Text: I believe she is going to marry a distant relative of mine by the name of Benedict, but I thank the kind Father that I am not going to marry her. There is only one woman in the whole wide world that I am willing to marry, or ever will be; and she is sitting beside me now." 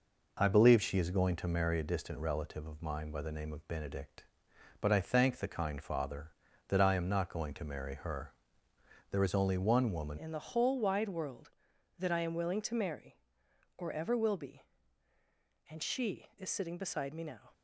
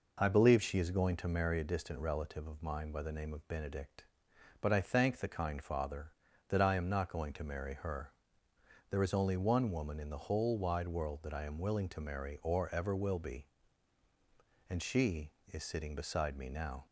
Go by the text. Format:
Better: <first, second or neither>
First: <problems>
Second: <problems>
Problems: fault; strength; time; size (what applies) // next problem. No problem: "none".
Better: second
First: changes voice at "in"; from 10.1 s on; 7.4 s long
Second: none